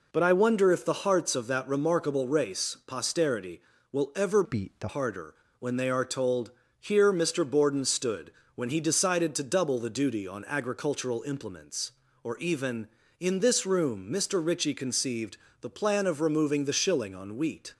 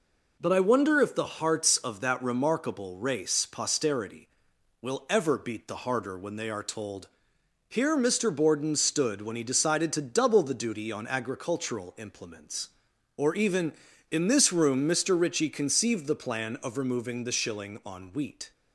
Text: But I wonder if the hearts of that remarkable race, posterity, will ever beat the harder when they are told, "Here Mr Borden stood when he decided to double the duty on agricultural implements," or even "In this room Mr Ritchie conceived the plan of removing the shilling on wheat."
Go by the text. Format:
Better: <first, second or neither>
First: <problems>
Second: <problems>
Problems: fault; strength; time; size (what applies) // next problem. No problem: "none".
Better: second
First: changes voice from "beat" to "the"; from 4.4 to 4.8 s; 0.4 s long // pauses between "harder" and "when"; slight; at 5.3 s; 0.26 s long // pauses between "stood" and "when"; slight; at 8.3 s; 0.24 s long // pauses between "conceived" and "the"; slight; at 15.3 s; 0.24 s long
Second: none